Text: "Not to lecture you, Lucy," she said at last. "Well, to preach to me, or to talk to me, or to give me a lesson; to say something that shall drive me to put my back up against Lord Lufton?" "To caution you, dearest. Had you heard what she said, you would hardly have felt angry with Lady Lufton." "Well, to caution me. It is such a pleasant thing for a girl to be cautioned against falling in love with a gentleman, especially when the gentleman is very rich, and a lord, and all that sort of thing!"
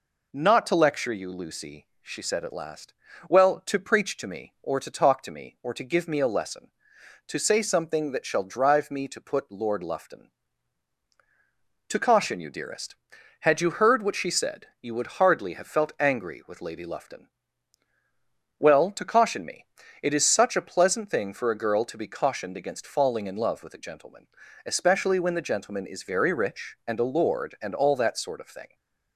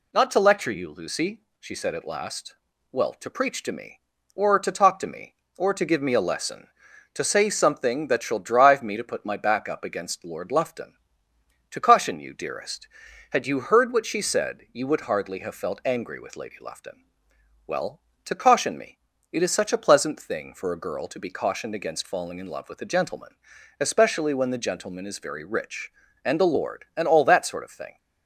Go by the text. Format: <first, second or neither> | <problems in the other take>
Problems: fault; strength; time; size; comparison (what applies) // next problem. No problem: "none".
second | skips "my back up against"; at 9.5 s